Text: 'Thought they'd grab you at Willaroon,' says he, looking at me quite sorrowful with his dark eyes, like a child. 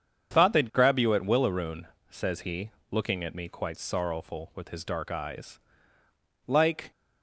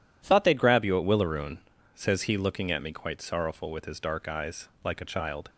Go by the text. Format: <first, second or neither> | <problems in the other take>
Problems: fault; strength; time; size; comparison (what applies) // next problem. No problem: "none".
second | starts louder than the rest; strong; until 1.3 s; 7.5 dB // stops before "a child"; at 6.9 s